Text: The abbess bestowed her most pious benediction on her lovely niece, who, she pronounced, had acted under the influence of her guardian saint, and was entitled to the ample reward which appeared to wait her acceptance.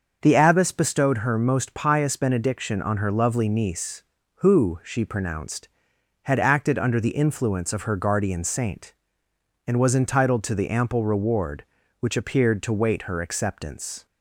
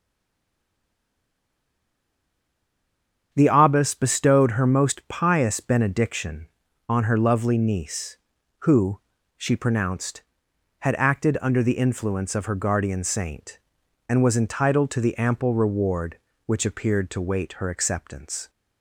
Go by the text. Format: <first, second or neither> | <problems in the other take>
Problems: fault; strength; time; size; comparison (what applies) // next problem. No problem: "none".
first | stays silent before the first word; strong; until 3.3 s; 3.3 s long // starts louder than the rest; strong; until 4.3 s; 7.5 dB; also in the first